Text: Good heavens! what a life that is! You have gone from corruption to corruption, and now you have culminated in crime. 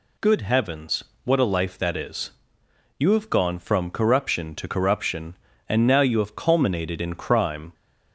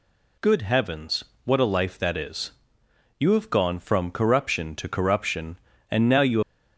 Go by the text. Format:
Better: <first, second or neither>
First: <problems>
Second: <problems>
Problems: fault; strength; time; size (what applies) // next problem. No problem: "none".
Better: first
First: none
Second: stops before "have culminated in crime"; at 6.4 s